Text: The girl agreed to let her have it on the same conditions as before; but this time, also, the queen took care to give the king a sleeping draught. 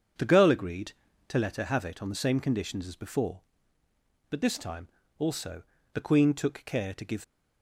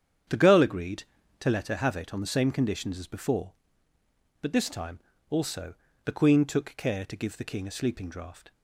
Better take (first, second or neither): second